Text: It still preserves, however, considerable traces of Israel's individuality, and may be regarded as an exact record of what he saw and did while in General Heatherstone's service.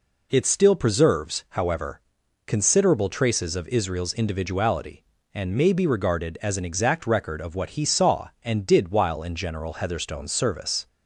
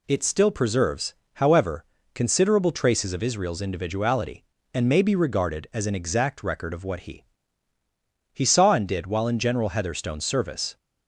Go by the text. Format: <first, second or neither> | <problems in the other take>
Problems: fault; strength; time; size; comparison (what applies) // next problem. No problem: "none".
first | says "he" twice; at 8.3 s